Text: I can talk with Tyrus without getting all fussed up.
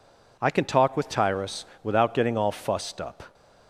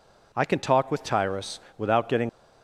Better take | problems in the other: first | pauses between "Tyrus" and "without"; slight; at 1.5 s; 0.16 s long; slight in the first // stops before "all fussed up"; at 2.2 s

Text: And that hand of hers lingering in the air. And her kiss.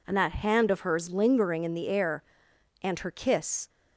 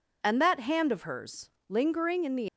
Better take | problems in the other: first | pauses between "hers" and "lingering"; slight; at 1.4 s; 0.18 s long // stops before "air And her kiss"; at 2.4 s

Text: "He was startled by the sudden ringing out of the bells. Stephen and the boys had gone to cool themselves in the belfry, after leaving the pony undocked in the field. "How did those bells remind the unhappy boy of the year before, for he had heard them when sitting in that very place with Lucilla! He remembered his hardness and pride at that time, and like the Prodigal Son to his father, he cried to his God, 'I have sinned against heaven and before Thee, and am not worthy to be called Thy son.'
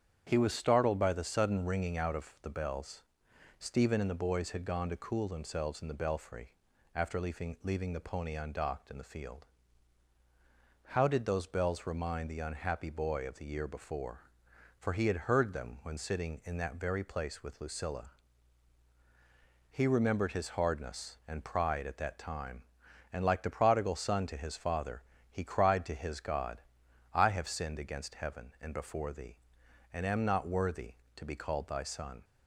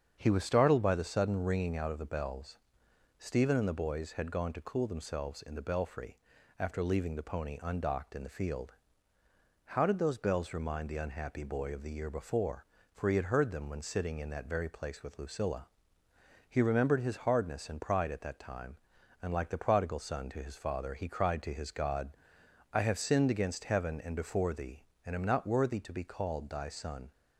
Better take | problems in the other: second | starts louder than the rest; strong; until 1.2 s; 8.5 dB; strong in the second // says "leaving" twice; at 7.6 s

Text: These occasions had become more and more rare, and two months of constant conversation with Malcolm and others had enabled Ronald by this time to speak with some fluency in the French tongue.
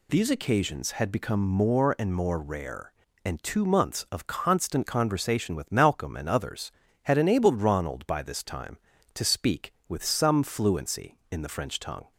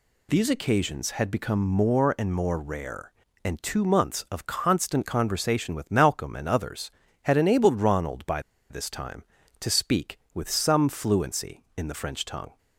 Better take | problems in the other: first | pauses between "by" and "this"; slight; at 8.3 s; 0.30 s long

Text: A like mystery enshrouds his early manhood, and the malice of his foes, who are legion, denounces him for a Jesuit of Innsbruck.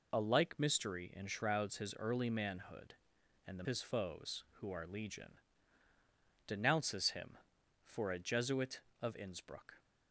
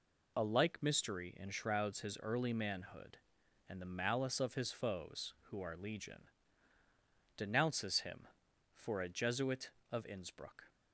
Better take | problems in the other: second | skips "malice of"; at 3.6 s

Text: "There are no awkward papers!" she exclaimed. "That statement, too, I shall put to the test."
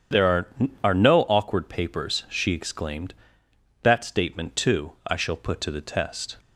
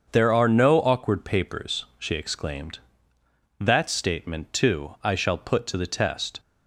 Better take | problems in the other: second | starts louder than the rest; strong; until 1.5 s; 8.5 dB; also in the second // says "are" twice; at 0.8 s

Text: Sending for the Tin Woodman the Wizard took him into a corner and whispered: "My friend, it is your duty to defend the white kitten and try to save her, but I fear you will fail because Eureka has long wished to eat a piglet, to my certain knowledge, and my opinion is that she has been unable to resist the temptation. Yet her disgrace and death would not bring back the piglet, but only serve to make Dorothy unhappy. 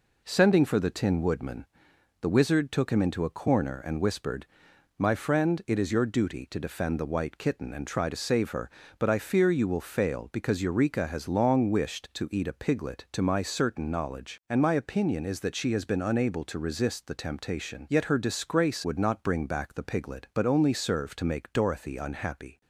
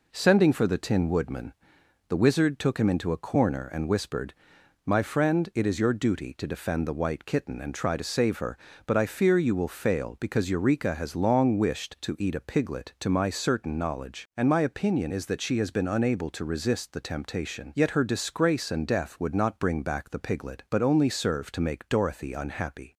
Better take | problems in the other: second | pauses between "Woodman" and "the"; noticeable; at 1.6 s; 0.56 s long; noticeable in the second // skips "and death"; at 18.8 s

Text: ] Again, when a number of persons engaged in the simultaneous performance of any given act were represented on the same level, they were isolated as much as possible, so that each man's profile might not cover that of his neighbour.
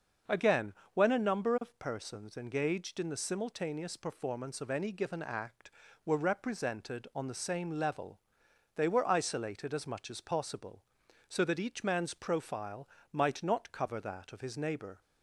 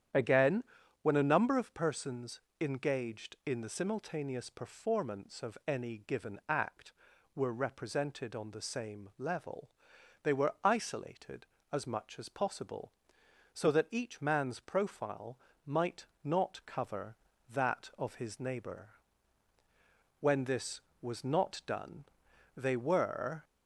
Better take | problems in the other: first | starts louder than the rest; strong; until 1.5 s; 9.5 dB; noticeable in the first // pauses between "persons" and "engaged"; slight; at 2.3 s; 0.20 s long // pauses between "profile" and "might"; slight; at 15.3 s; 0.28 s long; slight in the first // pauses between "might" and "not"; slight; at 16.0 s; 0.18 s long // goes on to say "When this was not done they were"; strong; from 20.1 s on; 3.2 s long

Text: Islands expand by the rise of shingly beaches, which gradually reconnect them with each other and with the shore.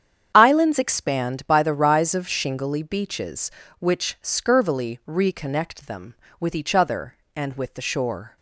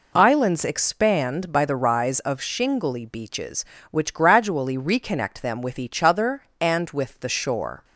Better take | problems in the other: second | starts louder than the rest; strong; until 1.3 s; 8.5 dB // says "scurvily" for "gradually"; at 4.2 s

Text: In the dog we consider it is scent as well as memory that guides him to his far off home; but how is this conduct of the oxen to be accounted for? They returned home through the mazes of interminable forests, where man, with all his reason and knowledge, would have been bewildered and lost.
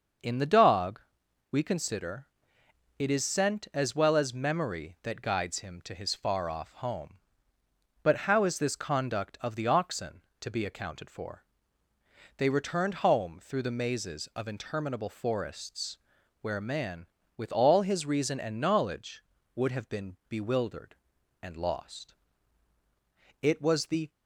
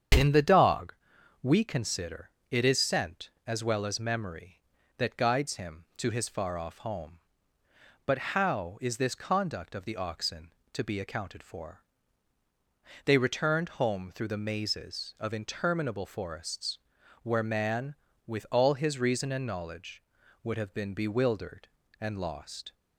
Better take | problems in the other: second | starts louder than the rest; until 1.7 s; 6.5 dB; strong in the second // pauses between "dog" and "we"; noticeable; at 1.0 s; 0.50 s long; noticeable in the second // pauses between "consider" and "it"; noticeable; at 2.2 s; 0.72 s long; slight in the second // goes on to say "It was the"; noticeable; from 23.4 s on; 0.66 s long

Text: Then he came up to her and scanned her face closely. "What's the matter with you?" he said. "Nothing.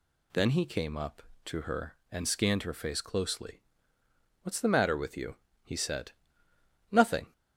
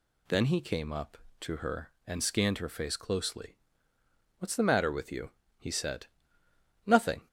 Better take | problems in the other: neither | none

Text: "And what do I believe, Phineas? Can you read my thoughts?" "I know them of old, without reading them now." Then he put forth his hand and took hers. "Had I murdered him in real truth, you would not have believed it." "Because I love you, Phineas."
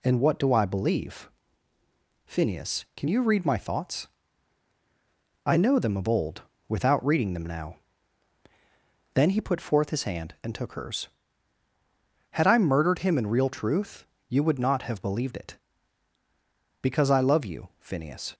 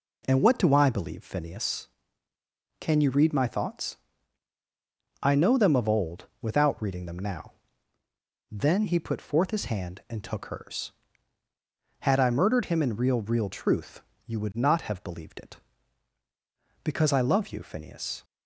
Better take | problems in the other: first | says "real" twice; at 13.1 s

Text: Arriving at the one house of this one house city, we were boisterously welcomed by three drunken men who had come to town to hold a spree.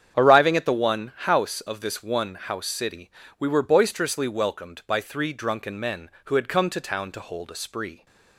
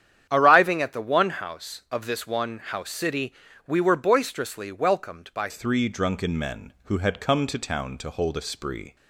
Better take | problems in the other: first | starts louder than the rest; strong; until 1.3 s; 9.5 dB; strong in the first // changes voice at "three"; from 5.4 s on; 3.5 s long

